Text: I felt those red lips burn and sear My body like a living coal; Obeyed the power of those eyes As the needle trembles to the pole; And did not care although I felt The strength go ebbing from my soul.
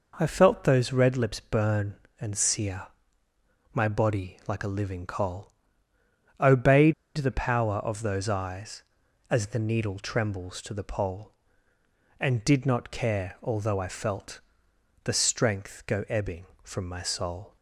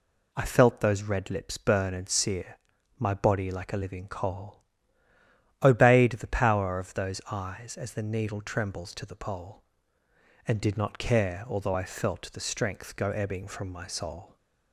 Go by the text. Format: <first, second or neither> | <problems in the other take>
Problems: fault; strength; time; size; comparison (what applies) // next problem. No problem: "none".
second | pauses between "sear" and "My"; noticeable; at 2.8 s; 0.86 s long; also in the second // pauses between "Obeyed" and "the"; slight; at 6.9 s; 0.24 s long // pauses between "felt" and "The"; noticeable; at 14.4 s; 0.62 s long